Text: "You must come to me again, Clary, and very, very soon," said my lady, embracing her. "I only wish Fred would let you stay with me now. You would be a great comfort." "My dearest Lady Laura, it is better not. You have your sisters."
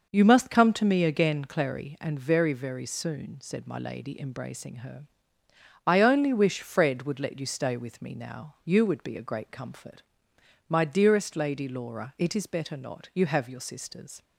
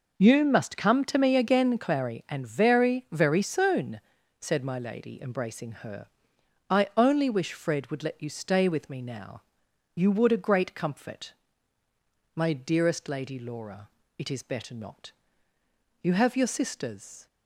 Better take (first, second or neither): first